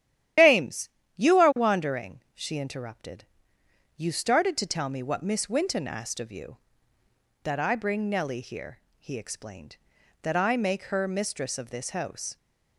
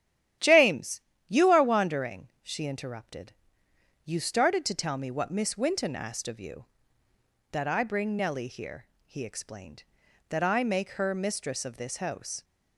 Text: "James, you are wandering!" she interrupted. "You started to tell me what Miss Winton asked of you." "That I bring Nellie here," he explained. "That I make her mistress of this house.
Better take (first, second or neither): second